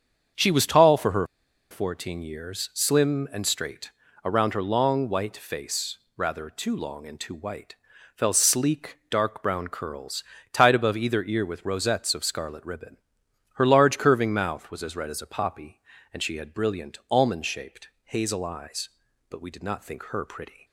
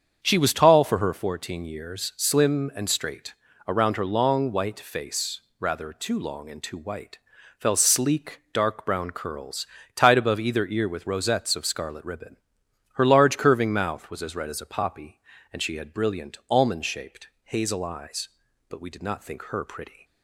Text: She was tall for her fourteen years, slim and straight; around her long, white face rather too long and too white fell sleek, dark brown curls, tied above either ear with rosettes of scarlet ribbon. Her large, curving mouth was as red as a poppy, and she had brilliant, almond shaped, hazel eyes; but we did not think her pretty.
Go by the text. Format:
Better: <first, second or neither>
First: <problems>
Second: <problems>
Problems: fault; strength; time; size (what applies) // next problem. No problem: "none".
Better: second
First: starts louder than the rest; strong; until 1.8 s; 7.5 dB // pauses between "her" and "fourteen"; at 1.2 s; 0.45 s long // pauses between "face" and "rather"; slight; at 5.9 s; 0.18 s long // pauses between "white" and "fell"; at 7.7 s; 0.42 s long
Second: starts louder than the rest; strong; until 1.2 s; 7.5 dB // pauses between "face" and "rather"; slight; at 5.3 s; 0.18 s long // pauses between "white" and "fell"; at 7.1 s; 0.42 s long